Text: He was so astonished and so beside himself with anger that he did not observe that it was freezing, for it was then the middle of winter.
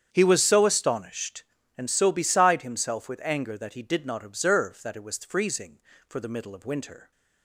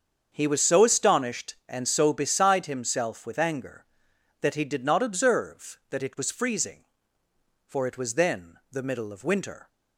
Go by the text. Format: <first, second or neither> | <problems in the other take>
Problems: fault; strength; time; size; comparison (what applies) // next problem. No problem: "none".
second | starts louder than the rest; strong; until 1.1 s; 8.5 dB; also in the second // skips "it was then"; at 6.1 s